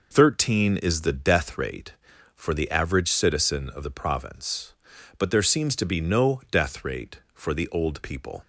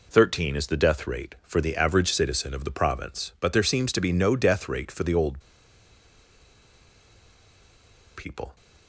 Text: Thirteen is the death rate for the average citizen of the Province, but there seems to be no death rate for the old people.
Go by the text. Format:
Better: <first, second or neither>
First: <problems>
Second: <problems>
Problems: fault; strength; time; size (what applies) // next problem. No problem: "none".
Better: first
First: none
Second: pauses between "old" and "people"; strong; at 5.3 s; 2.7 s long